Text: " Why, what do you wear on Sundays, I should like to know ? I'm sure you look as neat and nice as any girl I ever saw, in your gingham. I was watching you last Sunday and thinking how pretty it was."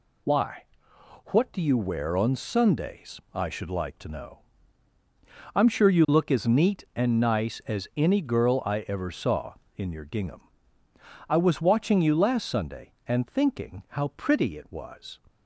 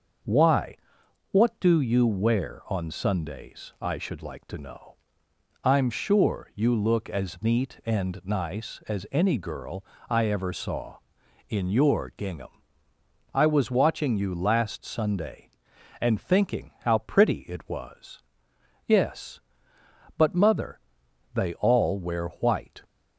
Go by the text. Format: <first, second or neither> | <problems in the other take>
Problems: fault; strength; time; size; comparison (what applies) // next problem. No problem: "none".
first | starts louder than the rest; until 1.7 s; 7 dB // pauses between "girl" and "I"; slight; at 9.8 s; 0.24 s long // goes on to say "Yes but mother they all wear white"; strong; from 18.8 s on; 3.9 s long